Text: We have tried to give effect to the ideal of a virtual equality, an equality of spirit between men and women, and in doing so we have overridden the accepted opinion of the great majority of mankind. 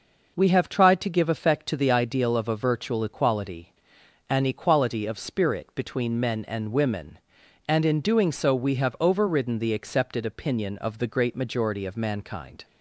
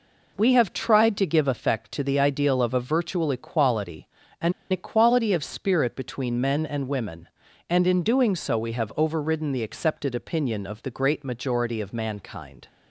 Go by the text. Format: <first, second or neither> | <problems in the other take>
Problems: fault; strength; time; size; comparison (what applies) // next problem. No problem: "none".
first | pauses between "an" and "equality"; slight; at 4.5 s; 0.18 s long